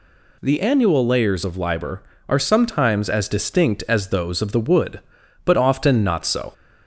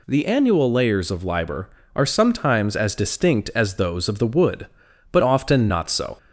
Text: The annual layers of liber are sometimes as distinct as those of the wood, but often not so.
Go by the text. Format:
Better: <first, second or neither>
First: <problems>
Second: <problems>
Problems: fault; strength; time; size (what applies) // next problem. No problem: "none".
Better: neither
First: none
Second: none